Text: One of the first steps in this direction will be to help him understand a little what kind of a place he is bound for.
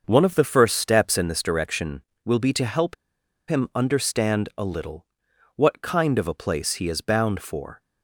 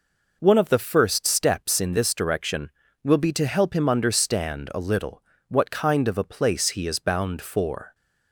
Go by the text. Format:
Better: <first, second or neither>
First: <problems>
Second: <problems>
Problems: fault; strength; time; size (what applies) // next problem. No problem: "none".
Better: second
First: starts louder than the rest; until 1.0 s; 6.5 dB // pauses between "help" and "him"; noticeable; at 2.9 s; 0.54 s long // pauses between "little" and "what"; noticeable; at 5.0 s; 0.50 s long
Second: pauses between "little" and "what"; slight; at 5.2 s; 0.26 s long